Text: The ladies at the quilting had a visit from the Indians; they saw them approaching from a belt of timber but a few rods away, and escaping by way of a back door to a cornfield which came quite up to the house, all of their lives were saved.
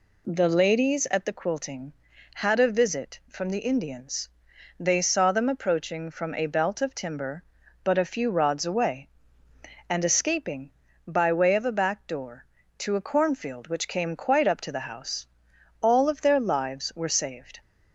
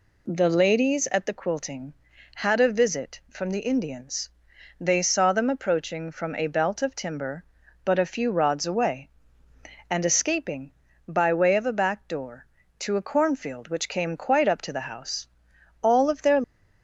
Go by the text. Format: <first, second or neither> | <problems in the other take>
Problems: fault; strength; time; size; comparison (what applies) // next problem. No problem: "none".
first | stops before "lives were saved"; at 16.4 s